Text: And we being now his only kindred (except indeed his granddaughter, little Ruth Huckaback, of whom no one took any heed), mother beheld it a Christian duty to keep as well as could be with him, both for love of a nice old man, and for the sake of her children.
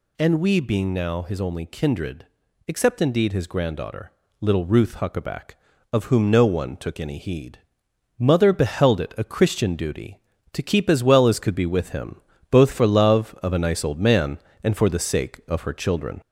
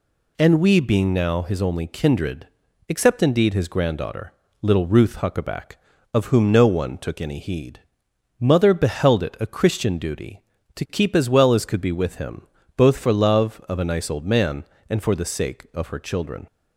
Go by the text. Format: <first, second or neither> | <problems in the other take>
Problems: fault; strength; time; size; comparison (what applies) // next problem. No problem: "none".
second | gets louder; slight; throughout; 3 dB